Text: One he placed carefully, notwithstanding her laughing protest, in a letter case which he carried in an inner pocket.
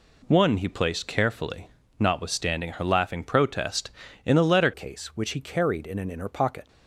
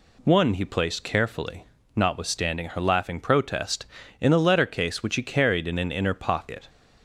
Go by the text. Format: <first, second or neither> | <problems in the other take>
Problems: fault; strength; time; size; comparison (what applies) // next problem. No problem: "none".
second | changes voice at "case"; from 4.7 s on; 1.9 s long